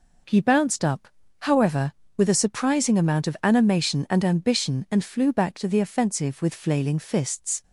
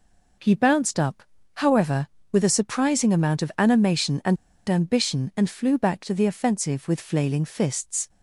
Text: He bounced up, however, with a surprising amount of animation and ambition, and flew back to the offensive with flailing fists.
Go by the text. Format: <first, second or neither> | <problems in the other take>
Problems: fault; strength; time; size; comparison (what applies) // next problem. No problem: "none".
first | pauses between "and" and "ambition"; slight; at 4.3 s; 0.32 s long